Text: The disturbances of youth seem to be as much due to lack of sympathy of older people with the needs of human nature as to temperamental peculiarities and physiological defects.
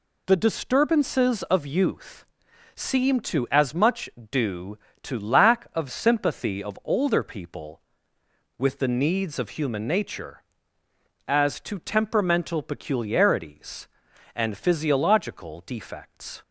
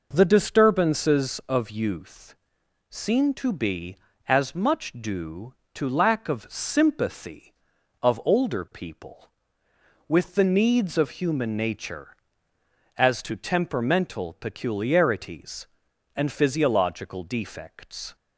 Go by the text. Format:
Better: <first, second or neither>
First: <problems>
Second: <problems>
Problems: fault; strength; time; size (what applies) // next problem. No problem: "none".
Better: second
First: pauses between "youth" and "seem"; noticeable; at 2.2 s; 0.50 s long // skips "be"; at 3.4 s // pauses between "much" and "due"; slight; at 4.0 s; 0.20 s long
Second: pauses between "youth" and "seem"; noticeable; at 2.3 s; 0.54 s long